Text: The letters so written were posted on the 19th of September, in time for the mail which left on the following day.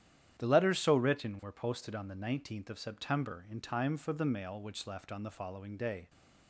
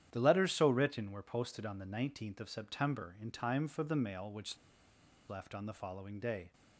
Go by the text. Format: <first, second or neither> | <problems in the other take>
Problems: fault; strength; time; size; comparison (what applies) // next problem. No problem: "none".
first | starts louder than the rest; strong; until 1.1 s; 10.5 dB; strong in the first // pauses between "which" and "left"; noticeable; at 4.5 s; 0.72 s long